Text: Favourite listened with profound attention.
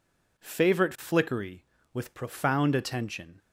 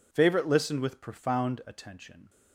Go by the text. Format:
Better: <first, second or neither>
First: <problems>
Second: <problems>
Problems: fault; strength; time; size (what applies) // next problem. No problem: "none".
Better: second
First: says "flickery" for "listened"; at 0.9 s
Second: none